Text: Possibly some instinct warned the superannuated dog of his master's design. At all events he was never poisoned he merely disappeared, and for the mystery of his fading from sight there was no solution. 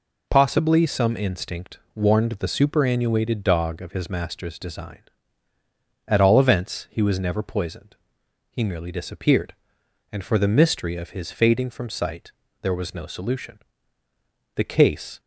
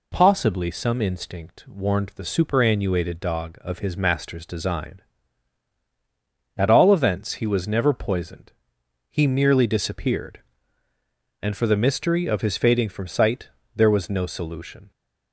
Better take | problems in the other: second | pauses between "instinct" and "warned"; slight; at 1.7 s; 0.16 s long // pauses between "poisoned" and "he"; noticeable; at 7.9 s; 0.54 s long; noticeable in the second // pauses between "sight" and "there"; slight; at 12.3 s; 0.30 s long; slight in the second // goes on to say "The case"; noticeable; from 14.5 s on; 0.64 s long

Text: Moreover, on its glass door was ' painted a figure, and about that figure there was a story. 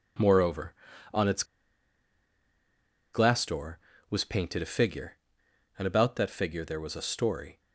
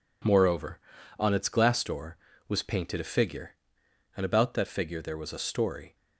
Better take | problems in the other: second | pauses between "its" and "glass"; strong; at 1.4 s; 1.7 s long

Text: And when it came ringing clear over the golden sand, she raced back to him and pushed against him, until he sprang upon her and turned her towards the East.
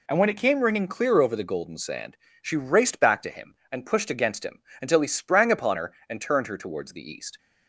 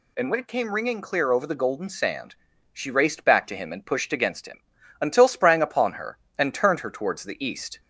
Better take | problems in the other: first | skips "he"; at 5.2 s

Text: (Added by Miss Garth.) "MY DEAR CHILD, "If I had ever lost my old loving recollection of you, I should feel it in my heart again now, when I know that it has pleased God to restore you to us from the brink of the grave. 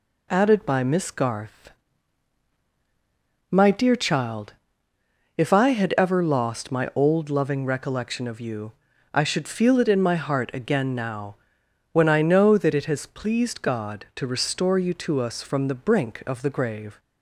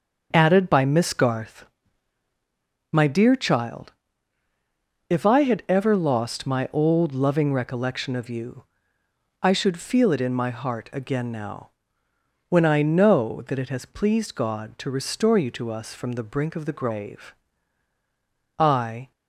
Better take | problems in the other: first | starts louder than the rest; until 1.3 s; 6.5 dB // goes on to say "I"; from 18.5 s on; 0.54 s long

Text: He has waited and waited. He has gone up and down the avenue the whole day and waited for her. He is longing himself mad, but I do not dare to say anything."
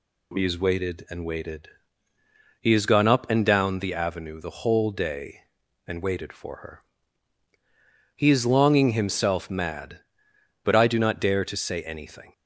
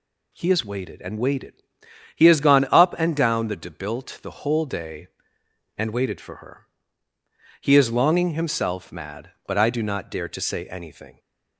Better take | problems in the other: first | says "debilt" for "avenue"; at 3.5 s

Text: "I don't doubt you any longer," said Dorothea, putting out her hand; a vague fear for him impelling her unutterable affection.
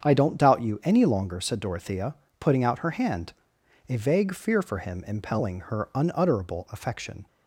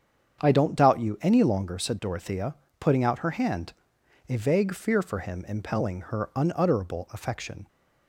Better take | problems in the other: neither | starts louder than the rest; strong; the same in both

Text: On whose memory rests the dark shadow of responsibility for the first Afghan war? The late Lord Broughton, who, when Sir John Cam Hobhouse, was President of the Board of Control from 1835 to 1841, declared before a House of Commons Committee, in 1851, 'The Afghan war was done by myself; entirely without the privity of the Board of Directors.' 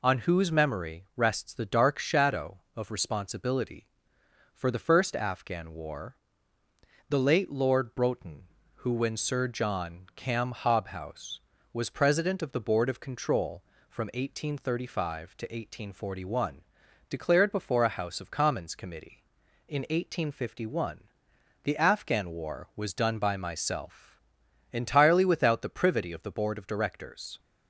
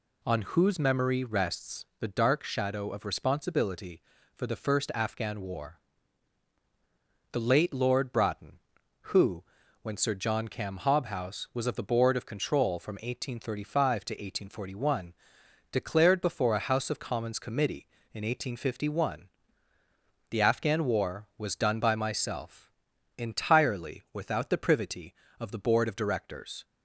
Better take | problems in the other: first | skips "President"; at 11.6 s

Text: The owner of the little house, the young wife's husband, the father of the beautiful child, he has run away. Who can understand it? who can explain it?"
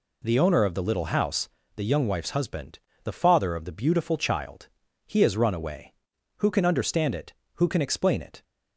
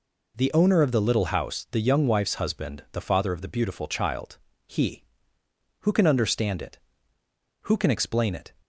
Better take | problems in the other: first | skips "has run away"; at 5.4 s

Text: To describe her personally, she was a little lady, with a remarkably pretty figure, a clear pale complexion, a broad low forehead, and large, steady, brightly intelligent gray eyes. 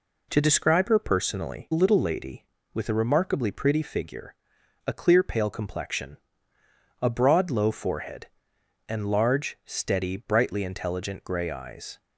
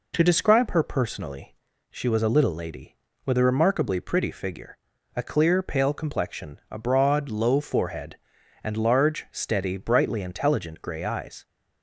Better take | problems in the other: second | skips "she was a"; at 1.7 s

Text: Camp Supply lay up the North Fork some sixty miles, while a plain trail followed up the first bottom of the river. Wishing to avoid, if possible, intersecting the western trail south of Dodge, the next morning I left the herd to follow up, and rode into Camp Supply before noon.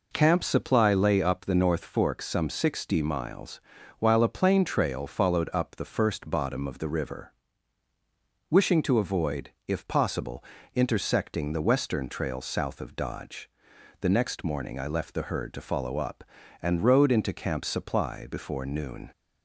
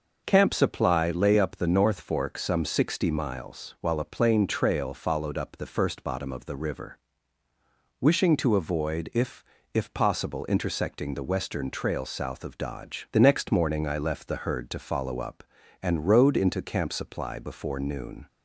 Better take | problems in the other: first | says "if" twice; at 9.7 s

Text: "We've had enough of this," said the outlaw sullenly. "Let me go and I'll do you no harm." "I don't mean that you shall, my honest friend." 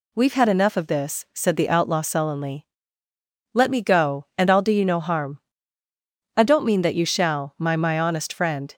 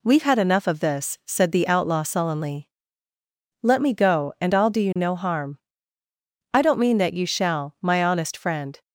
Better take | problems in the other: second | says "my" twice; at 7.7 s

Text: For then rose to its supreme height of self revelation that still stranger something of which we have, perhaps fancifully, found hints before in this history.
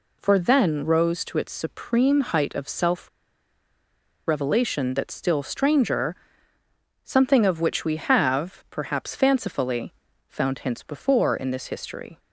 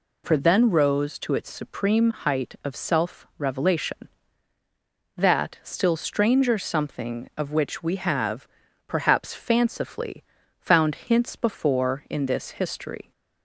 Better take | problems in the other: second | pauses between "self" and "revelation"; at 3.0 s; 1.1 s long // pauses between "stranger" and "something"; noticeable; at 6.1 s; 0.90 s long

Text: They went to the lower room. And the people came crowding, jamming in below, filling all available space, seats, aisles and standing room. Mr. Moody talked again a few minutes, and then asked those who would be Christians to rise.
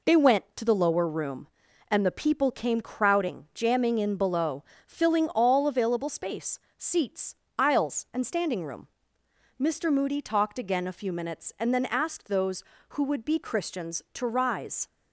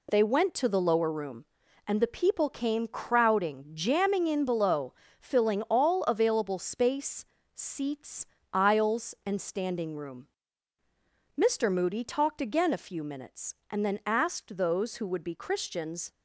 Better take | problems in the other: first | stops before "to rise"; at 16.1 s

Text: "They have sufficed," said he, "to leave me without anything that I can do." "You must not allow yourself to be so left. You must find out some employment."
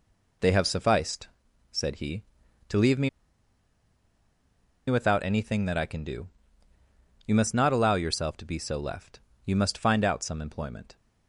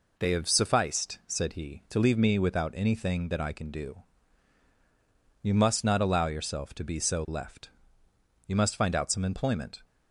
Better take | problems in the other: second | pauses between "me" and "without"; strong; at 3.0 s; 1.7 s long

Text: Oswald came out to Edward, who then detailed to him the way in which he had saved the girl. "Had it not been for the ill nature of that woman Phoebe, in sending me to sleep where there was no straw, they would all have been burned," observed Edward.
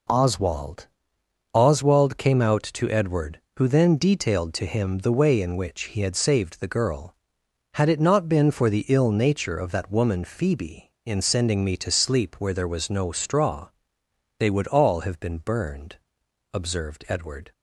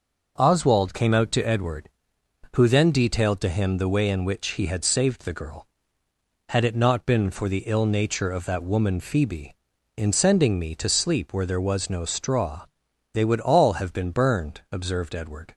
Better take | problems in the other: second | says "Oswald" twice; at 1.5 s

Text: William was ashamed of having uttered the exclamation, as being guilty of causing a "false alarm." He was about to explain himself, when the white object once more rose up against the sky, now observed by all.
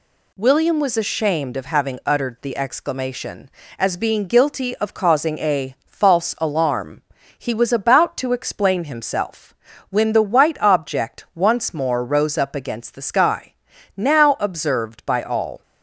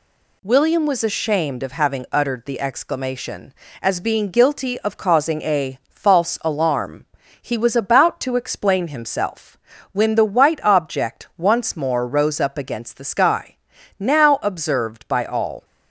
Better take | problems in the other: neither | none

